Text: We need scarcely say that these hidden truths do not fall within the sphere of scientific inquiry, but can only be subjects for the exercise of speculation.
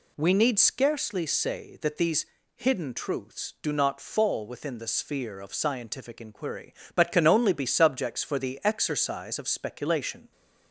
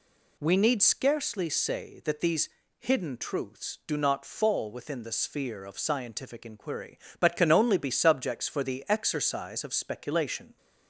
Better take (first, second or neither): neither